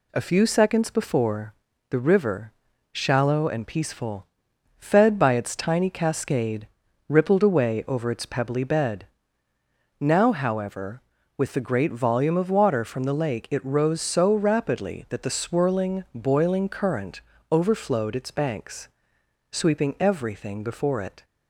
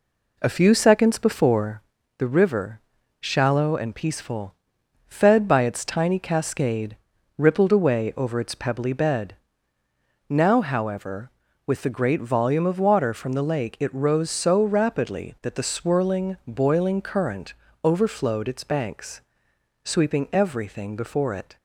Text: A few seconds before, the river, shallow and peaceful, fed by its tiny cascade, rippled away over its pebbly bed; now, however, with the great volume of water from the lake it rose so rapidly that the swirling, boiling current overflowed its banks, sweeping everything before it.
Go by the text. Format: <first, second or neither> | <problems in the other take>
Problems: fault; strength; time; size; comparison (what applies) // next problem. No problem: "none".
first | starts louder than the rest; slight; until 1.9 s; 3 dB // pauses between "current" and "overflowed"; slight; at 17.5 s; 0.32 s long; slight in the first